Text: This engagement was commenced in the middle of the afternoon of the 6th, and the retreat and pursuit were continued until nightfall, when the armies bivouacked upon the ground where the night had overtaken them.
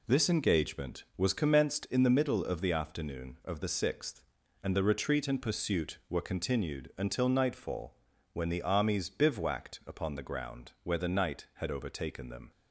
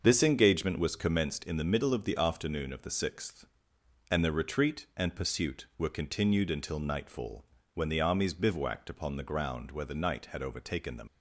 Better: first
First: none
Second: starts louder than the rest; until 1.0 s; 6 dB // leaves "them" unfinished; at 11.0 s; 50 ms

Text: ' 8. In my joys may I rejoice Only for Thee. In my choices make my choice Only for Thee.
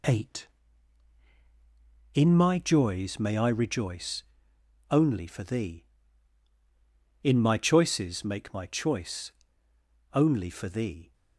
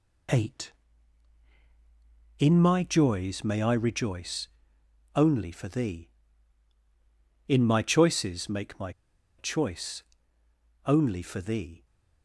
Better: first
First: pauses between "rejoice" and "Only"; noticeable; at 4.2 s; 0.68 s long // pauses between "choice" and "Only"; noticeable; at 9.3 s; 0.80 s long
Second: pauses between "rejoice" and "Only"; noticeable; at 4.4 s; 0.68 s long // pauses between "my" and "choice"; noticeable; at 8.9 s; 0.46 s long // pauses between "choice" and "Only"; noticeable; at 10.0 s; 0.82 s long

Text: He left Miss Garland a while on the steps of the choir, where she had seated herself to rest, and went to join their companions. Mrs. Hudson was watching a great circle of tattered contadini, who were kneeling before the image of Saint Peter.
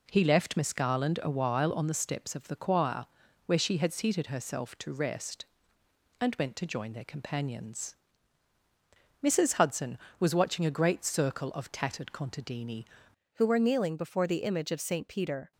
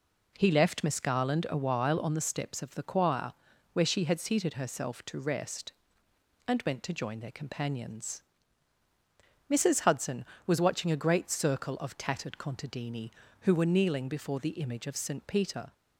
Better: second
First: changes voice at "who"; from 13.3 s on; 2.2 s long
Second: none

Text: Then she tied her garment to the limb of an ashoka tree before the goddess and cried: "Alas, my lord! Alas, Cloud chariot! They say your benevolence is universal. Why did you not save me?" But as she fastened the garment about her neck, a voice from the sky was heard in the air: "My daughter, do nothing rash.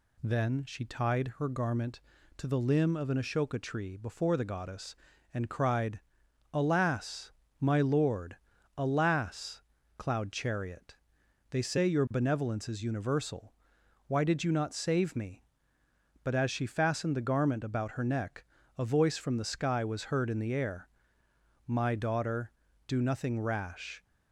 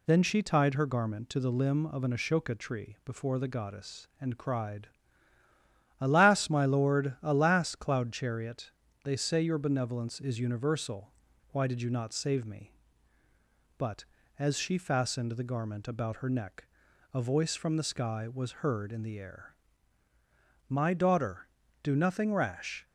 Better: neither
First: none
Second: none

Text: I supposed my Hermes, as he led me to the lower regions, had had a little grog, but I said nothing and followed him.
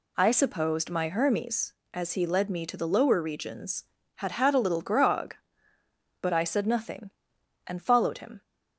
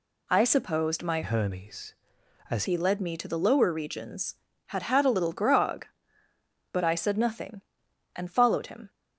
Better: first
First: none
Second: changes voice from "Hermes" to "as"; from 1.2 to 2.6 s; 1.4 s long

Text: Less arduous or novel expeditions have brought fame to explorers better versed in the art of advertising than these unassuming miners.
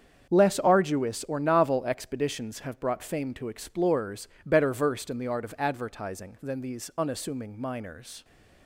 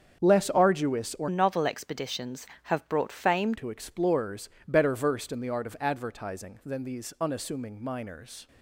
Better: first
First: starts louder than the rest; strong; until 1.3 s; 7.5 dB // pauses between "explorers" and "better"; slight; at 4.2 s; 0.17 s long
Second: starts louder than the rest; strong; until 1.2 s; 7.5 dB // changes voice from "novel" to "fame"; from 1.2 to 3.5 s; 2.3 s long // pauses between "explorers" and "better"; slight; at 4.4 s; 0.18 s long

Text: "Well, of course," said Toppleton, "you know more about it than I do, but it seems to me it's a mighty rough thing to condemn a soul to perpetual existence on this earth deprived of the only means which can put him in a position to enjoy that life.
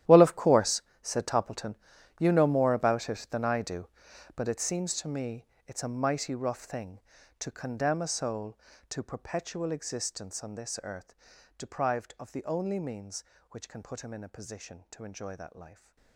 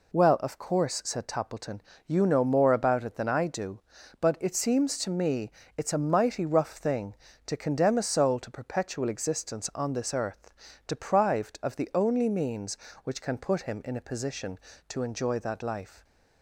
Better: second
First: gets quieter; strong; throughout; 17.5 dB // pauses between "me" and "it's"; slight; at 5.4 s; 0.20 s long // pauses between "earth" and "deprived"; at 11.1 s; 0.42 s long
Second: pauses between "me" and "it's"; slight; at 5.5 s; 0.24 s long // pauses between "earth" and "deprived"; slight; at 10.5 s; 0.34 s long

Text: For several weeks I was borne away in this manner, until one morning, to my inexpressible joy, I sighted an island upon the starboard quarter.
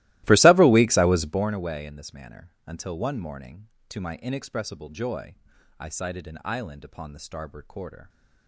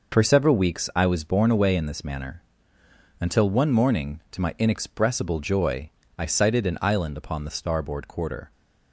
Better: second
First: starts louder than the rest; strong; until 1.5 s; 17.5 dB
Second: none

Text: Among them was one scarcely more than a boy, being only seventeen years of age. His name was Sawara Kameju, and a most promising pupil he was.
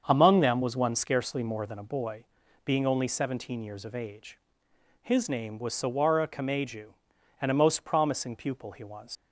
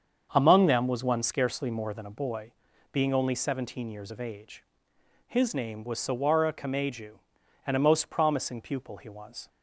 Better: second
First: starts louder than the rest; until 1.0 s; 7 dB // leaves "was" unfinished; at 9.1 s; 75 ms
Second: starts louder than the rest; until 1.3 s; 7 dB

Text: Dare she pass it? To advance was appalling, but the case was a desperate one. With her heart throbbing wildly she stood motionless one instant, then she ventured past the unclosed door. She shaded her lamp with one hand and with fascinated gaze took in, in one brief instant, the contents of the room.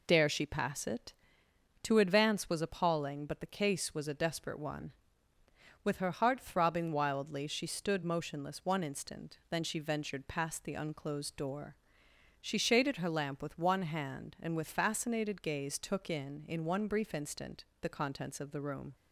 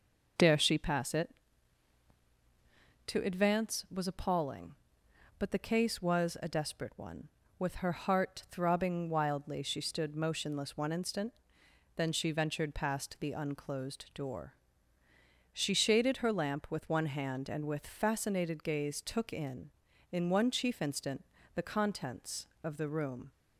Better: first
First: none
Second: says "chief" for "brief"; at 20.5 s

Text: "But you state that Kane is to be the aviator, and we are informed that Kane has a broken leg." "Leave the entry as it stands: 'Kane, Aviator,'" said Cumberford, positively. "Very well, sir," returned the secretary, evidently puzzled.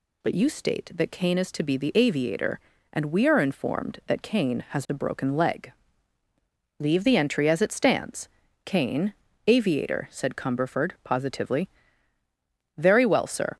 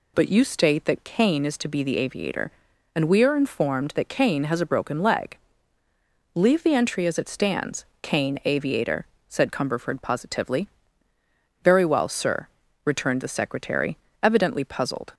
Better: second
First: stops before "returned the secretary evidently puzzled"; at 13.5 s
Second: none

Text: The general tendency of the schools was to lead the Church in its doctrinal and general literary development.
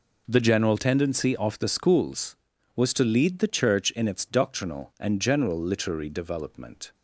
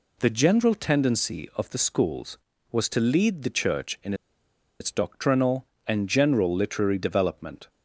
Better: first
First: none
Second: pauses between "in" and "its"; noticeable; at 4.1 s; 0.66 s long

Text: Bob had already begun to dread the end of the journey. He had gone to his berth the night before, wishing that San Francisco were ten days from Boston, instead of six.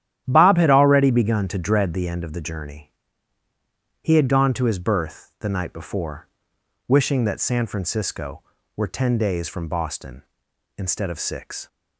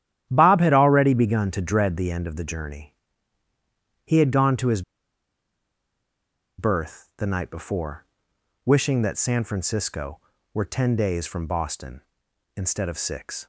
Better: first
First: starts louder than the rest; strong; until 1.2 s; 11 dB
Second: starts louder than the rest; strong; until 1.3 s; 11 dB // pauses between "his" and "berth"; strong; at 4.8 s; 1.7 s long

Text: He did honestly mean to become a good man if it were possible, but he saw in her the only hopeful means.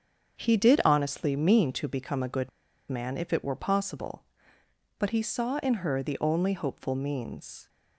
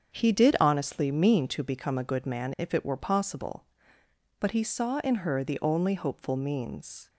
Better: second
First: starts louder than the rest; until 1.4 s; 7 dB // pauses between "good" and "man"; at 2.4 s; 0.40 s long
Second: starts louder than the rest; strong; until 1.2 s; 7 dB

